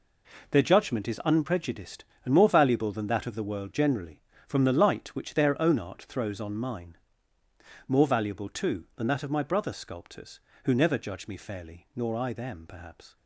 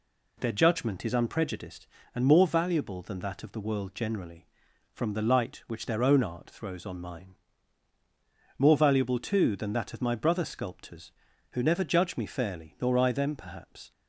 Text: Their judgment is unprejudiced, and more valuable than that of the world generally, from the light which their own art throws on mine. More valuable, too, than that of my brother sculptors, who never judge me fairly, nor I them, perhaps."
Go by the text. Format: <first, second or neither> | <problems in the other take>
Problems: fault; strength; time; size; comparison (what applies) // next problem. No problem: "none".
neither | none